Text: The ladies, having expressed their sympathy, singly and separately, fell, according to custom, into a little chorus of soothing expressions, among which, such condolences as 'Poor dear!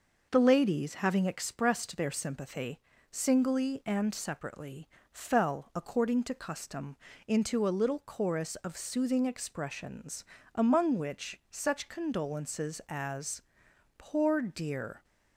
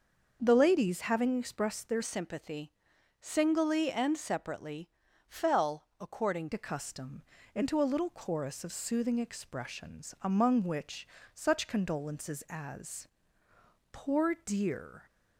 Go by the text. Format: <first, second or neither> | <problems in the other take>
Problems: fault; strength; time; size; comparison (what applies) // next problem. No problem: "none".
first | starts louder than the rest; until 1.4 s; 6.5 dB // changes voice from "sympathy" to "according"; from 2.0 to 6.4 s; 4.4 s long // pauses between "as" and "Poor"; noticeable; at 13.0 s; 0.82 s long; noticeable in the first